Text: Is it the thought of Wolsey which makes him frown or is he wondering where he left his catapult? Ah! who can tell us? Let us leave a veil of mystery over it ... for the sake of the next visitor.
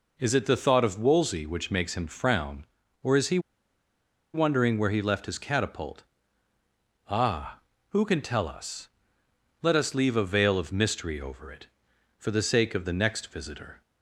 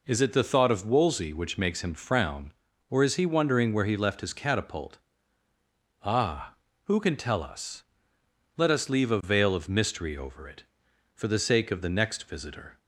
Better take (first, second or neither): second